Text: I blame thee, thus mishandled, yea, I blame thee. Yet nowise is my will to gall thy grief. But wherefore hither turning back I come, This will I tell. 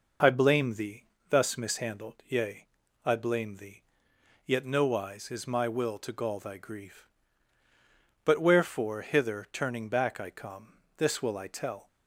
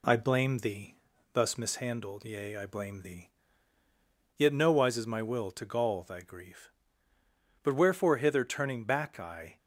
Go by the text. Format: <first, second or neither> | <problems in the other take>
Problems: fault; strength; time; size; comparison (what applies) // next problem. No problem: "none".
first | stops before "come This will I tell"; at 9.5 s